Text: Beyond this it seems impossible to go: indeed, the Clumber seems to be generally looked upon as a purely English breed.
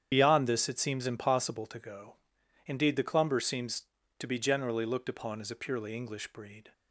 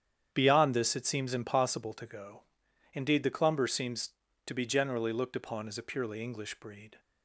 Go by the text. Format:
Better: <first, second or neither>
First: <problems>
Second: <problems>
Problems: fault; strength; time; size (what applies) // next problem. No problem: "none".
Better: second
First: loses the start of "Beyond"; at 0.1 s; 55 ms // starts louder than the rest; strong; until 1.1 s; 9 dB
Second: starts louder than the rest; strong; until 1.3 s; 9 dB